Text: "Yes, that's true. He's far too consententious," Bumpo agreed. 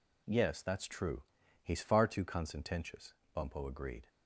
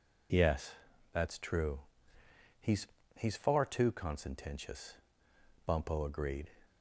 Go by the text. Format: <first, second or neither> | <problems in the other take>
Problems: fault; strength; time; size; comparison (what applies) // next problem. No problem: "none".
first | says "He's" twice; at 3.1 s